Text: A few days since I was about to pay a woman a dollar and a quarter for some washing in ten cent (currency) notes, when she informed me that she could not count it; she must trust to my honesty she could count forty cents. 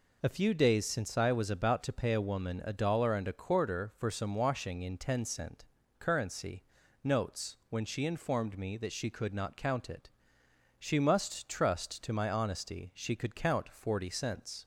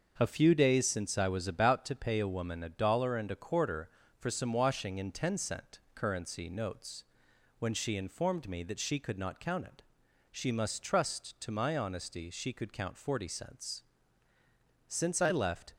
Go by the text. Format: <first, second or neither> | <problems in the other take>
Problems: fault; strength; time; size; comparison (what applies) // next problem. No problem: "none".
first | starts louder than the rest; until 1.1 s; 6 dB // goes on to say "Since I left"; noticeable; from 14.8 s on; 0.86 s long